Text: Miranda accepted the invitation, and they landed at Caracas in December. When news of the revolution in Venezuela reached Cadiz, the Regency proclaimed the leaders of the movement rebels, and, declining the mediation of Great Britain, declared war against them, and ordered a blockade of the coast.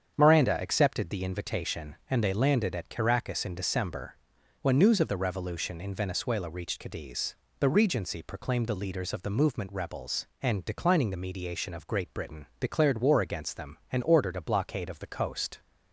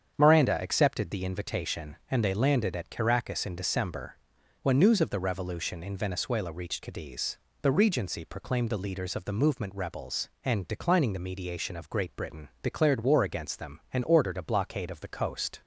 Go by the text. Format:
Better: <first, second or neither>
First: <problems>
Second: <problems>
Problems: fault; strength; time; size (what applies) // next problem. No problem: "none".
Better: neither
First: starts louder than the rest; strong; until 1.1 s; 8 dB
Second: starts louder than the rest; strong; until 1.1 s; 8 dB